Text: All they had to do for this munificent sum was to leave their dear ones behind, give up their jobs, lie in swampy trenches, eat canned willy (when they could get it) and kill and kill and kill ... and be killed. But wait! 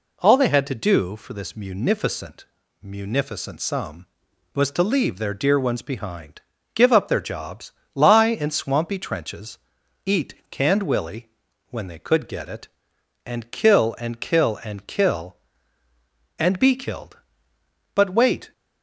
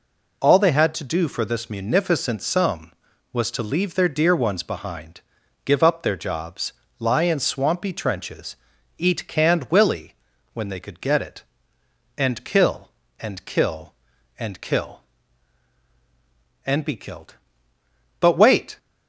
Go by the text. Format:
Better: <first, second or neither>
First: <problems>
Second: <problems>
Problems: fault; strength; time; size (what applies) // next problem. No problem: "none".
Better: second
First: says "munificent" twice; at 2.8 s // pauses between "eat" and "canned"; slight; at 10.3 s; 0.16 s long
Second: none